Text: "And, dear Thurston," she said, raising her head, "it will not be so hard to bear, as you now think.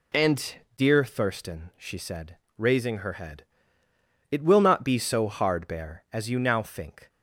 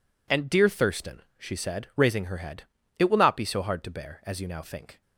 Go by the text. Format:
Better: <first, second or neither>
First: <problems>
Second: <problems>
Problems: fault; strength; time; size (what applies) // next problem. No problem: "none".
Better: second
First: skips "to"; at 5.6 s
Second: none